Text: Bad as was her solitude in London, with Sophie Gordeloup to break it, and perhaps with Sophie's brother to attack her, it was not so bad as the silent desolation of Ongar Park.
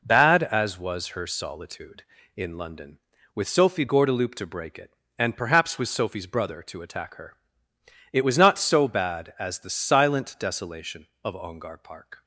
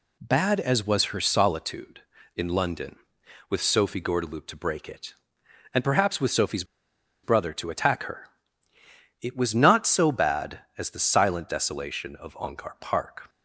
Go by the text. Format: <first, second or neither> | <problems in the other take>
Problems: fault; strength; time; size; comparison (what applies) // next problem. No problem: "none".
first | pauses between "Sophie's" and "brother"; noticeable; at 6.6 s; 0.59 s long